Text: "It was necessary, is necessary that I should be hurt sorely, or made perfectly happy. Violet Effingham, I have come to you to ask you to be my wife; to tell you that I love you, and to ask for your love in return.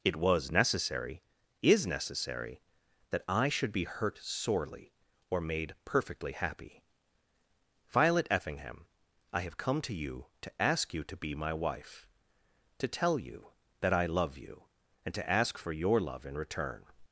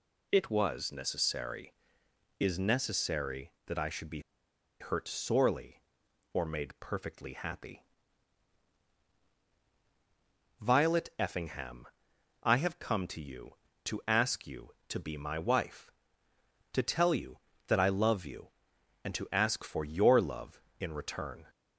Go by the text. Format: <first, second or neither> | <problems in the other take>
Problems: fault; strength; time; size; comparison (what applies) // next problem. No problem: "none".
first | pauses between "be" and "hurt"; noticeable; at 4.1 s; 0.60 s long